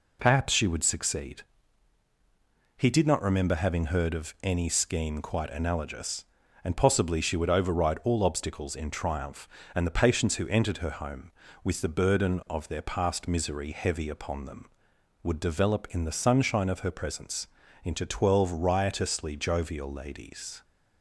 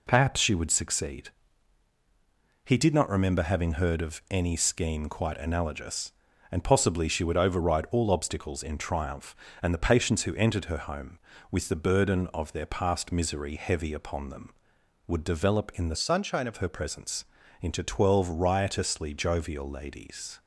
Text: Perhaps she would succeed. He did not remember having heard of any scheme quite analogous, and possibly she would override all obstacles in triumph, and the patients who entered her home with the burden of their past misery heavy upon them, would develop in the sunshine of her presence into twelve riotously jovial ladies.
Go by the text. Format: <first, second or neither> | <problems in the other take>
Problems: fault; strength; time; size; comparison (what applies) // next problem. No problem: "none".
first | changes voice from "sunshine" to "of"; from 15.9 to 16.5 s; 0.6 s long // pauses between "presence" and "into"; slight; at 17.2 s; 0.36 s long; slight in the first